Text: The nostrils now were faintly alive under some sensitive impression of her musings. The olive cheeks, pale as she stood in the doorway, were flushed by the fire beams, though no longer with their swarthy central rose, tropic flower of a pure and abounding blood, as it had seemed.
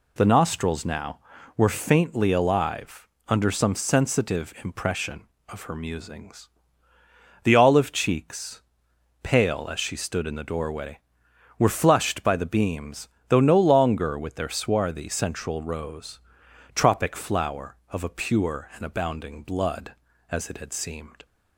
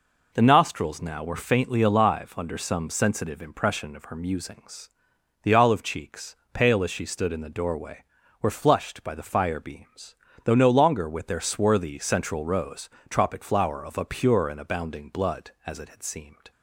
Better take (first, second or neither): second